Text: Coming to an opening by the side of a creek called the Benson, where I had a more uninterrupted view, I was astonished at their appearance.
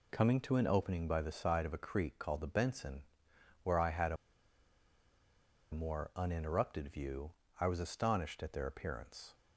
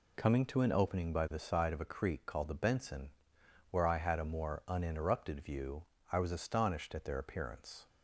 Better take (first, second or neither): second